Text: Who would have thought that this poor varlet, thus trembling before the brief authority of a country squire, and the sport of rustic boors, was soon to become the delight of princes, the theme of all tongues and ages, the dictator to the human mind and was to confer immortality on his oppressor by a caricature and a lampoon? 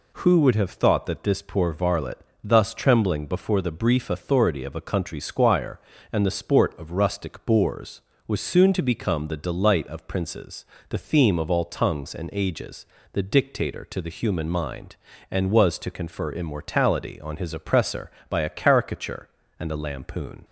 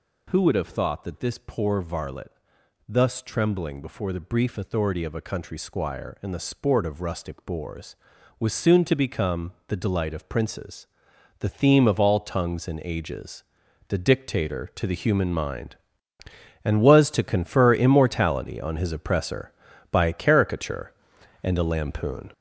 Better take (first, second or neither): first